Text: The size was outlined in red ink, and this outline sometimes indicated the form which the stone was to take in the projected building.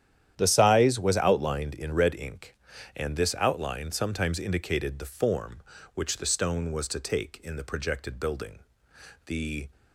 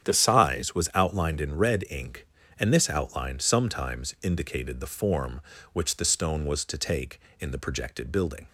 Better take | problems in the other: second | starts louder than the rest; strong; until 1.3 s; 10.5 dB; strong in the second // goes on to say "The"; slight; from 9.2 s on; 0.42 s long

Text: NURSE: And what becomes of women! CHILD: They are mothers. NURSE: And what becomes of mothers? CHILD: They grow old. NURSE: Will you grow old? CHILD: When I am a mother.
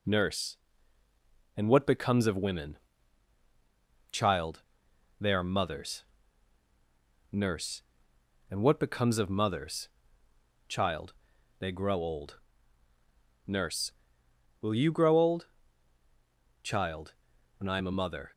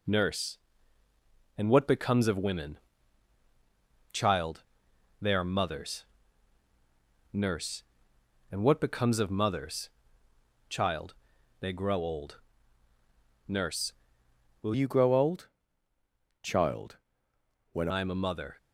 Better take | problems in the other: first | changes voice from "you" to "When"; from 14.7 to 17.8 s; 3.1 s long

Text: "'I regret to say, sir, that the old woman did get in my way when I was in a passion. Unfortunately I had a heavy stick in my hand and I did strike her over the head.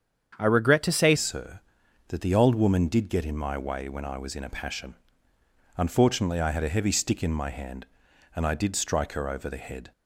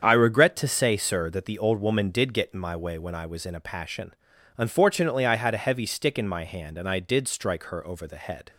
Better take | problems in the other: second | starts louder than the rest; strong; until 1.4 s; 8 dB; strong in the second // changes voice at "sir"; from 1.1 s on; 8.8 s long

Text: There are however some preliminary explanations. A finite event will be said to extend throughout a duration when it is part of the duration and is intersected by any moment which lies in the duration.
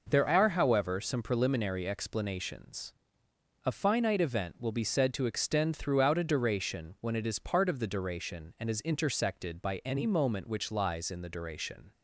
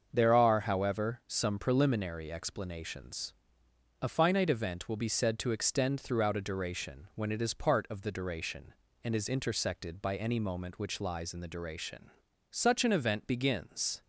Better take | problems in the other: first | starts louder than the rest; until 1.1 s; 6.5 dB // goes on to say "Such an event begins"; from 12.4 s on; 1.5 s long

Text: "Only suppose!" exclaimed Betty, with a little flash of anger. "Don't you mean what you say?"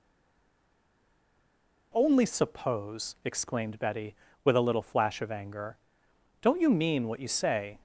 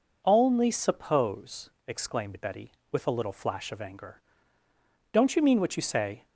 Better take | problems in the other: second | stays silent before the first word; noticeable; until 1.9 s; 1.9 s long

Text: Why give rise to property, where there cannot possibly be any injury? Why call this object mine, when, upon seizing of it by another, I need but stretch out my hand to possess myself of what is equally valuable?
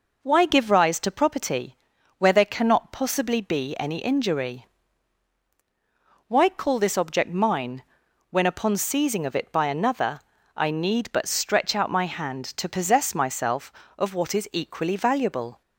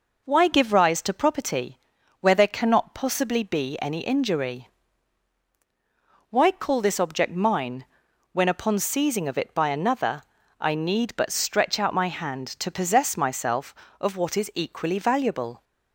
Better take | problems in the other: neither | none

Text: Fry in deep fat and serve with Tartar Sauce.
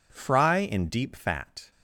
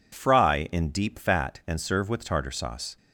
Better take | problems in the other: second | stops before "and serve with Tartar Sauce"; at 1.7 s

